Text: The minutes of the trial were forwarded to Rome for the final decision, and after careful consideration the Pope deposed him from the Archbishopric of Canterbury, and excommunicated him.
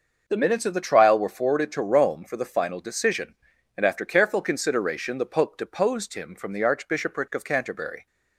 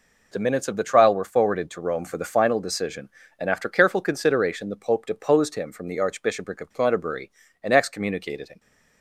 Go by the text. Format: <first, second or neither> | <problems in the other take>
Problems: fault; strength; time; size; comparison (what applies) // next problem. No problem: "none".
second | starts louder than the rest; noticeable; until 1.2 s; 6 dB // stops before "and excommunicated him"; at 8.0 s